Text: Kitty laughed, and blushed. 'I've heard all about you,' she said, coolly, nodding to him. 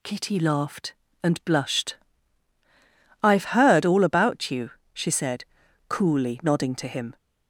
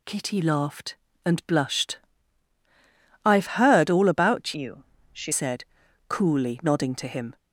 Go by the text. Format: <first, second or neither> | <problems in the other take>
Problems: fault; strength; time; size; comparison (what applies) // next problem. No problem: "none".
first | changes voice from "you" to "she"; from 4.5 to 5.3 s; 0.8 s long